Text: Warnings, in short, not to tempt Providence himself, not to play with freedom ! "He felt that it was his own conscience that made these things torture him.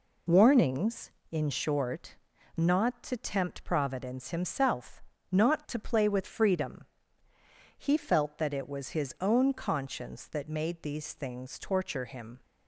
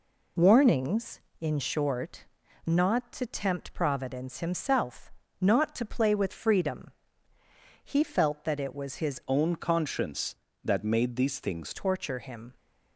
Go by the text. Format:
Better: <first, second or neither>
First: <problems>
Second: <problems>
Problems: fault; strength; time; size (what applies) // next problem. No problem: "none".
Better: first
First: none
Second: changes voice from "own" to "things"; from 9.2 to 11.7 s; 2.5 s long